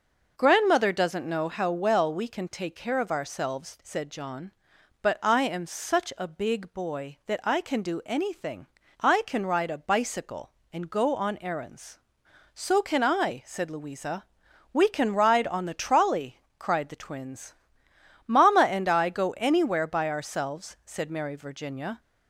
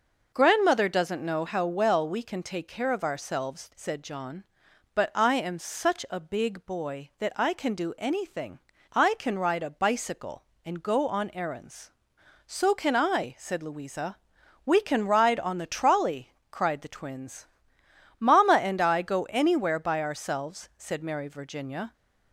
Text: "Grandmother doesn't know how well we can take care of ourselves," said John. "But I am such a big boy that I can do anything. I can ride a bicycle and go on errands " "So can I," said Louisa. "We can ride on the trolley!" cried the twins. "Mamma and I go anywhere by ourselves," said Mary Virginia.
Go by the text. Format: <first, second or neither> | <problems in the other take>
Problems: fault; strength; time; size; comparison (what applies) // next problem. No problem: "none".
neither | none